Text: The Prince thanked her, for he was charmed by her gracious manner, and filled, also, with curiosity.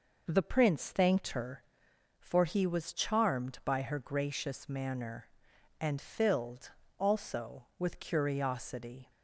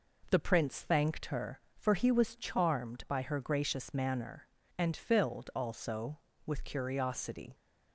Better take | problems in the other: neither | none

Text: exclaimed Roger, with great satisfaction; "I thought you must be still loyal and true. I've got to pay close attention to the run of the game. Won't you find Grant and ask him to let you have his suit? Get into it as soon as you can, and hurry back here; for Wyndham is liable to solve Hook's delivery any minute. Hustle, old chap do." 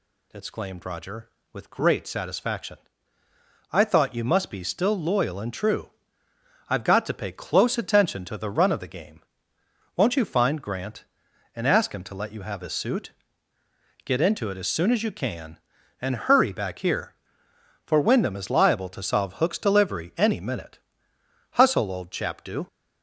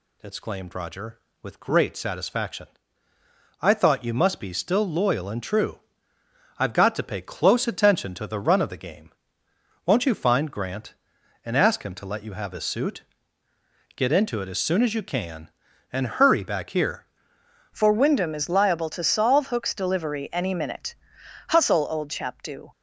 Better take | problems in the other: first | changes voice at "for"; from 17.7 s on; 5.0 s long

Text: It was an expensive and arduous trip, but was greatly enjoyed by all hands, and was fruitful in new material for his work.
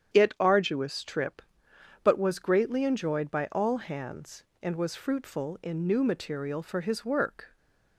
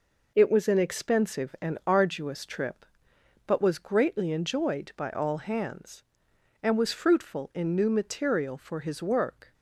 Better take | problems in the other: second | starts louder than the rest; strong; until 1.1 s; 9 dB // skips "was an expensive and"; at 0.3 s // stays silent after the last word; slight; from 7.4 s on; 0.5 s long

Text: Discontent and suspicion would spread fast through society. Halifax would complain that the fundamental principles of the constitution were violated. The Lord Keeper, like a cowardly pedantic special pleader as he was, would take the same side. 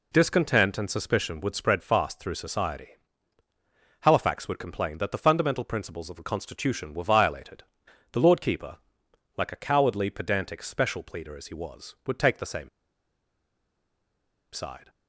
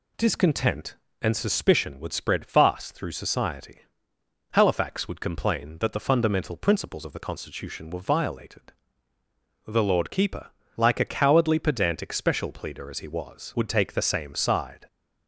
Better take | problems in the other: second | pauses between "same" and "side"; strong; at 12.6 s; 1.8 s long

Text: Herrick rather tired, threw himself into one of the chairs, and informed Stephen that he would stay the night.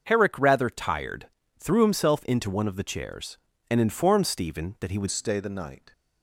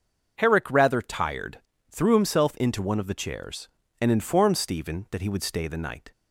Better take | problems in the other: second | starts louder than the rest; until 1.0 s; 6.5 dB // changes voice at "stay"; from 5.1 s on; 0.8 s long

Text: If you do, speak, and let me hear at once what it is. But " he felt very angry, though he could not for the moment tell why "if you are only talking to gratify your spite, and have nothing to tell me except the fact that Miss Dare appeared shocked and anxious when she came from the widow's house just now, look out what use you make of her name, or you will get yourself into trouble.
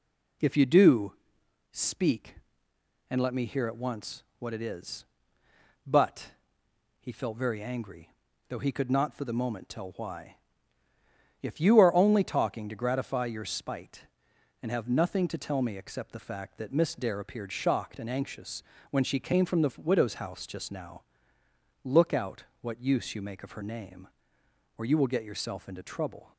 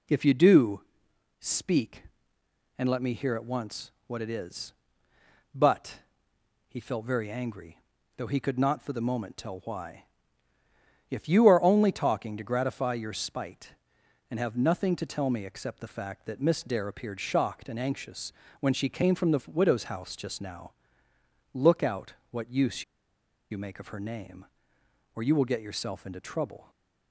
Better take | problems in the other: first | pauses between "once" and "what"; slight; at 3.9 s; 0.16 s long; slight in the first // pauses between "why" and "if"; at 10.0 s; 1.0 s long; also in the first // pauses between "anxious" and "when"; slight; at 18.3 s; 0.30 s long; slight in the first // pauses between "out" and "what"; slight; at 22.1 s; 0.18 s long; slight in the first // pauses between "use" and "you"; noticeable; at 22.8 s; 0.67 s long // stays silent after the last word; slight; from 26.6 s on; 0.5 s long

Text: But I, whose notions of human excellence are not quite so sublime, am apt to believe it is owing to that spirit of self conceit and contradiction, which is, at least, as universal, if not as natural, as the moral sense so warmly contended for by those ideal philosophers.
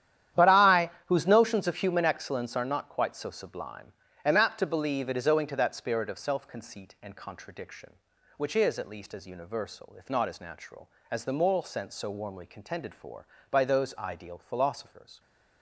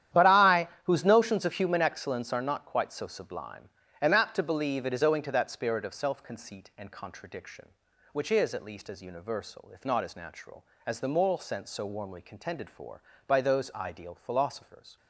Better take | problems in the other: neither | starts louder than the rest; strong; the same in both

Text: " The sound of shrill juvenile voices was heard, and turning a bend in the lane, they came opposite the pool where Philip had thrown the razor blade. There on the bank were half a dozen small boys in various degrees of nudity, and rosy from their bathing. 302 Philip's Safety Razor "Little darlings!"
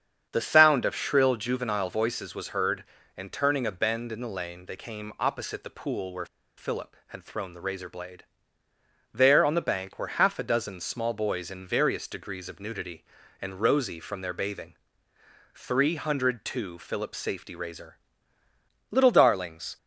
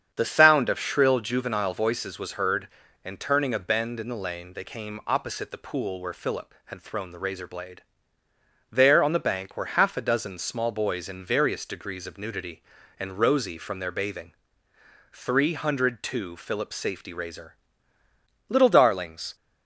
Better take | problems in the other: second | starts louder than the rest; strong; until 1.3 s; 8 dB; strong in the second // pauses between "where" and "Philip"; slight; at 6.2 s; 0.30 s long // pauses between "Razor" and "Little"; noticeable; at 17.9 s; 0.94 s long; noticeable in the second

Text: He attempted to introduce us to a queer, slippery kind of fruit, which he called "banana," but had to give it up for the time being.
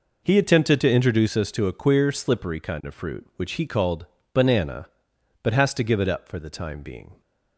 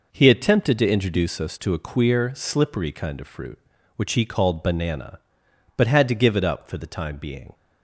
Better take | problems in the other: second | pauses between "called" and "banana"; slight; at 4.0 s; 0.26 s long // says "has" for "had"; at 5.5 s

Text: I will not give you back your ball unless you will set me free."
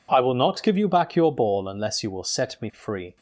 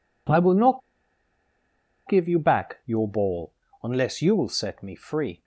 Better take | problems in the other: first | pauses between "not" and "give"; strong; at 0.8 s; 1.2 s long // pauses between "ball" and "unless"; slight; at 3.5 s; 0.30 s long

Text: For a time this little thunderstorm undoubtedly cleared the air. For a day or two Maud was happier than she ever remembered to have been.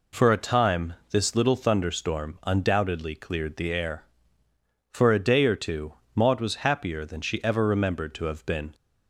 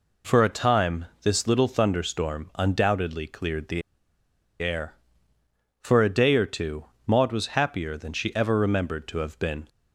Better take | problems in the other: first | pauses between "time" and "this"; slight; at 1.0 s; 0.16 s long; slight in the first // pauses between "the" and "air"; noticeable; at 3.8 s; 0.80 s long // pauses between "two" and "Maud"; slight; at 6.8 s; 0.20 s long; slight in the first

